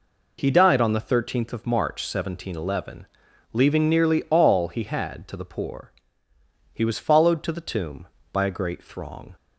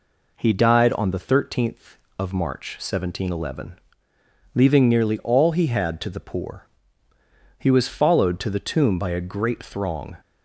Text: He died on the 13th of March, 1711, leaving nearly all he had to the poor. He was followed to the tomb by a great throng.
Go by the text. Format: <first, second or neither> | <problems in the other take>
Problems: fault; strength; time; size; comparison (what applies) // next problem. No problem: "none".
neither | none